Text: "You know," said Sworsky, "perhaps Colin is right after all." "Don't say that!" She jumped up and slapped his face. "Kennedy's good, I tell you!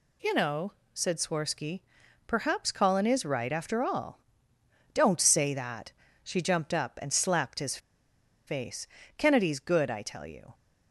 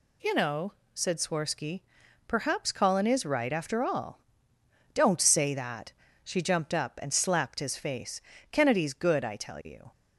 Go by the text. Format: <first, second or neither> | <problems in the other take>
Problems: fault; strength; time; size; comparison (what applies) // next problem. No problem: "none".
second | pauses between "his" and "face"; noticeable; at 7.7 s; 0.69 s long